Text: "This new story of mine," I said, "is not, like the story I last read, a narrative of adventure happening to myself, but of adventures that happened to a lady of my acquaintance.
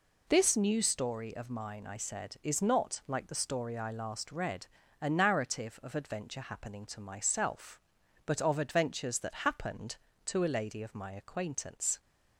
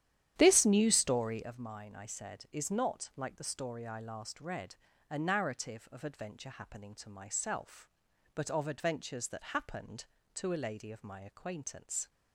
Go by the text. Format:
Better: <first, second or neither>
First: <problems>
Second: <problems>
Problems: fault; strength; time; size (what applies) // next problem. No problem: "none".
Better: first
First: none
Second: starts louder than the rest; strong; until 1.5 s; 11 dB